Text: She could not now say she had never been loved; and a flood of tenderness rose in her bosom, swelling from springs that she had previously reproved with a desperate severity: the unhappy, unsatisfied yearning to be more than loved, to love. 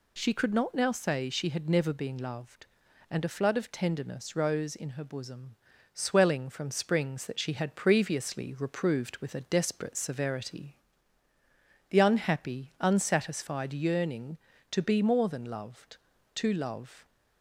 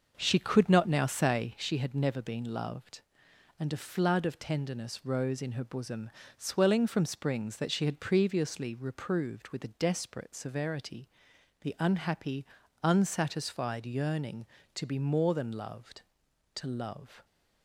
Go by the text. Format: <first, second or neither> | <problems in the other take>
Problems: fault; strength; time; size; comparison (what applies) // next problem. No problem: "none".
first | starts louder than the rest; noticeable; until 1.7 s; 6 dB